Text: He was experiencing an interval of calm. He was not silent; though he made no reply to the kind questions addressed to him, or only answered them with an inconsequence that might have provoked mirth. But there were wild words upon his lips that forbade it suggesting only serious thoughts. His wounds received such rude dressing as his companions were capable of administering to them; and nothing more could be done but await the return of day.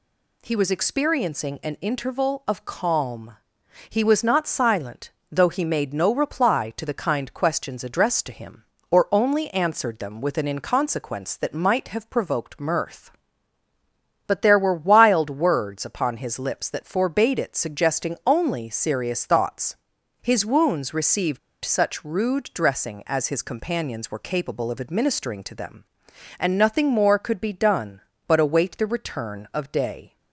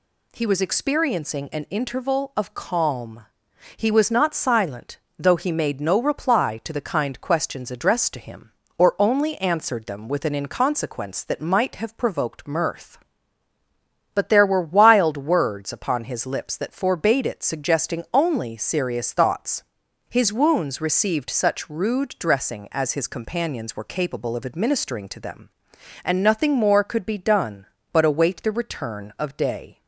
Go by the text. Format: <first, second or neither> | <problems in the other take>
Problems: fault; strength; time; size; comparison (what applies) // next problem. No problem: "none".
second | pauses between "received" and "such"; slight; at 21.3 s; 0.23 s long